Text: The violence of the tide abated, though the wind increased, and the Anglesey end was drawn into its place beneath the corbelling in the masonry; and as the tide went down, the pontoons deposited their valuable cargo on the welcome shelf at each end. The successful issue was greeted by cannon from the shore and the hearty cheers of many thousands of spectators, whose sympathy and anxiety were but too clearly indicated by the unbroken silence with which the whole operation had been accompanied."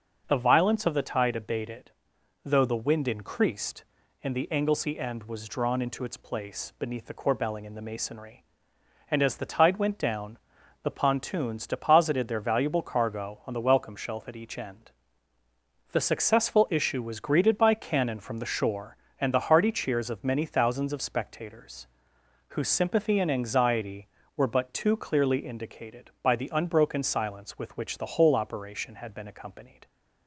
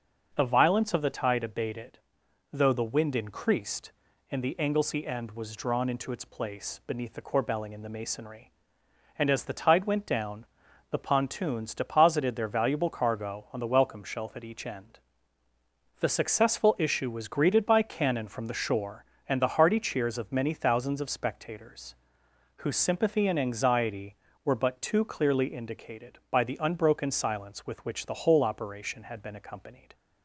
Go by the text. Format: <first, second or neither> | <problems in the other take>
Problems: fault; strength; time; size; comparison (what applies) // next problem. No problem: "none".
neither | starts louder than the rest; the same in both